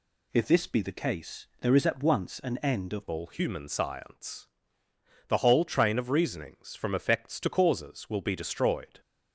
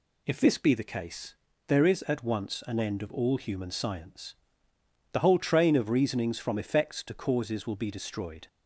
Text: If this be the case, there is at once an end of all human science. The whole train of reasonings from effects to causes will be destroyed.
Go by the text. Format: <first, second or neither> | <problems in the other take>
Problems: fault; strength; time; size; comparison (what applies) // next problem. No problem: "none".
second | changes voice at "all"; from 3.1 s on; 5.9 s long